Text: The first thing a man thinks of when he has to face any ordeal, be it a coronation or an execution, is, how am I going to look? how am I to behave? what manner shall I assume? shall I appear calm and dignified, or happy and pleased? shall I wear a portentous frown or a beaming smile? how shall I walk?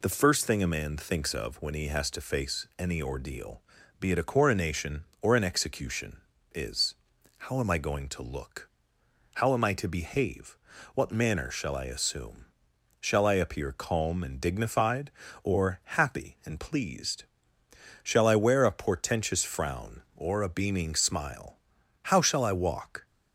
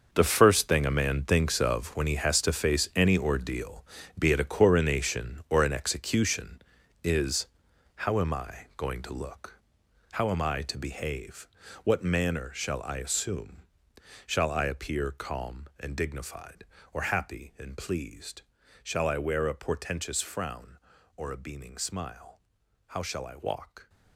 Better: first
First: none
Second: gets quieter; strong; throughout; 13 dB

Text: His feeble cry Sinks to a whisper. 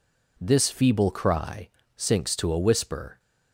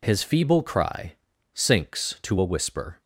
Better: second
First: says "This" for "His"; at 0.3 s // pauses between "cry" and "Sinks"; slight; at 1.6 s; 0.30 s long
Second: pauses between "cry" and "Sinks"; at 1.1 s; 0.40 s long

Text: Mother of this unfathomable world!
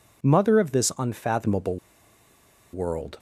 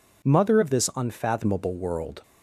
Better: second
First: pauses between "unfathomable" and "world"; noticeable; at 1.7 s; 0.96 s long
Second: none

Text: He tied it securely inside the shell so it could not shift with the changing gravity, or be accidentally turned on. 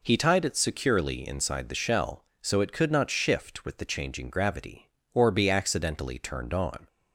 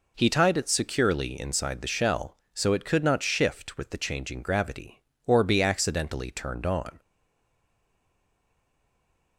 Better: first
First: none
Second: stays silent after the last word; from 6.9 s on; 2.4 s long

